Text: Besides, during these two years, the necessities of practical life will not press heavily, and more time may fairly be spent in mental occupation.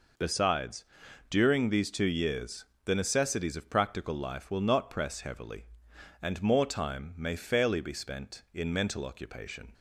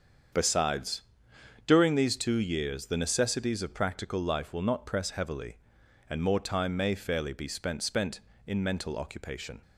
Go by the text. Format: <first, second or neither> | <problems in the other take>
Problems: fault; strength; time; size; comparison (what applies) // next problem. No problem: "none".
first | starts louder than the rest; strong; until 2.0 s; 7.5 dB // says "spent" twice; at 7.8 s